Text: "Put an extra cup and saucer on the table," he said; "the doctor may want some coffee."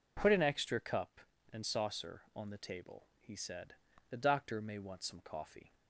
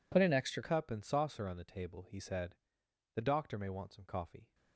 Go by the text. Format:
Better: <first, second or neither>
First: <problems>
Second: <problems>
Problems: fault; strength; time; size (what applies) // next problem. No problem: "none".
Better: first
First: none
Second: changes voice at "cup"; from 0.6 s on; 3.9 s long